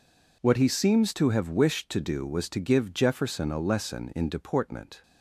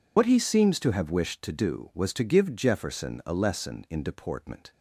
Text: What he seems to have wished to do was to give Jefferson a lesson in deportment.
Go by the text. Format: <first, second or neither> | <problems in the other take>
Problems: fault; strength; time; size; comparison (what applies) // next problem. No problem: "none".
first | loses the start of "What"; at 0.1 s; 70 ms